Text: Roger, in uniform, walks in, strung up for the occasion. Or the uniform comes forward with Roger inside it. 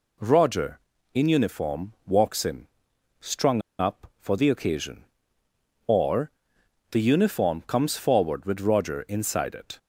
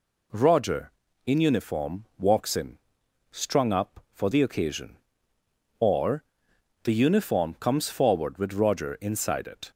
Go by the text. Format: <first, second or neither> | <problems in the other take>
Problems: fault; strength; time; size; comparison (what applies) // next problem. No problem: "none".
second | pauses between "strung" and "up"; slight; at 3.6 s; 0.18 s long // pauses between "Or" and "the"; noticeable; at 6.2 s; 0.60 s long; noticeable in the second